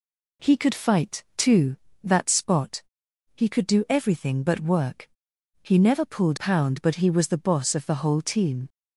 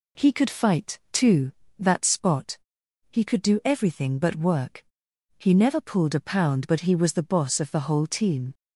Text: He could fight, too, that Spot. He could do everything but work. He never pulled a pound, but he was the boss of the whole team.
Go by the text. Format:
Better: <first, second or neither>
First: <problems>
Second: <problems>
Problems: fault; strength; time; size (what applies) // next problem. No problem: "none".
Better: second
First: skips "a"; at 6.3 s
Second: none